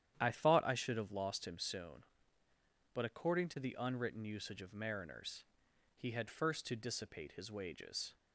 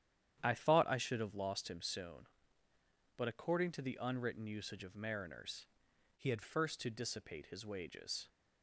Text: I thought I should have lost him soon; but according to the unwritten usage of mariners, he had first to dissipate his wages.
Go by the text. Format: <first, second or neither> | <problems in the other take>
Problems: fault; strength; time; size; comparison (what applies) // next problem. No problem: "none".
first | starts louder than the rest; strong; until 1.4 s; 10 dB; strong in the first // changes voice from "he" to "had"; from 6.1 to 6.4 s; 0.3 s long